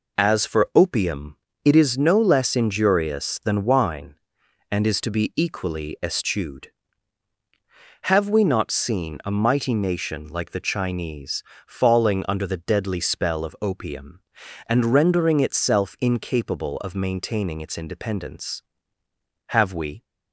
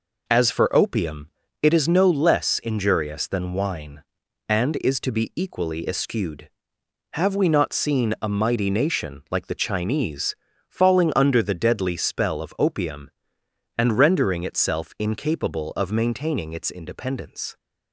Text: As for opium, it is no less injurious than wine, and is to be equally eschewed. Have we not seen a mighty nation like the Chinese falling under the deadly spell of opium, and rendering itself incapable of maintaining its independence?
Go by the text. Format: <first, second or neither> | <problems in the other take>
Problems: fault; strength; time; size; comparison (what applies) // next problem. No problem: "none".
second | pauses between "Chinese" and "falling"; slight; at 11.4 s; 0.24 s long; slight in the second // goes on to say "Have we"; from 19.4 s on; 0.56 s long